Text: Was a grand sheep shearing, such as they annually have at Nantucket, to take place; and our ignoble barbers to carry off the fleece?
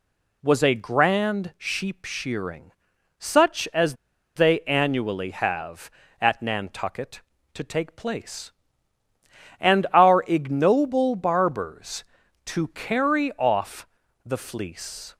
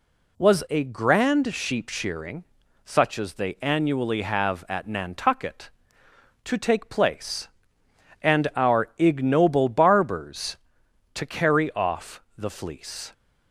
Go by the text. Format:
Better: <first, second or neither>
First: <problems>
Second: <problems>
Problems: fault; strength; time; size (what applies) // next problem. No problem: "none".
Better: second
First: pauses between "as" and "they"; at 3.9 s; 0.40 s long // pauses between "off" and "the"; slight; at 13.8 s; 0.36 s long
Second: pauses between "off" and "the"; slight; at 12.2 s; 0.16 s long